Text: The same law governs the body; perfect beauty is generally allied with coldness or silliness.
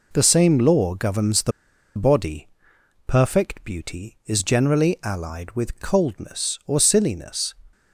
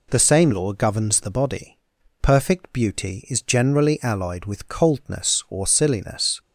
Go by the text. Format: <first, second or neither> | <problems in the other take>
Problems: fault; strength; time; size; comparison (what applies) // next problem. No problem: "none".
second | pauses between "the" and "body"; noticeable; at 1.5 s; 0.46 s long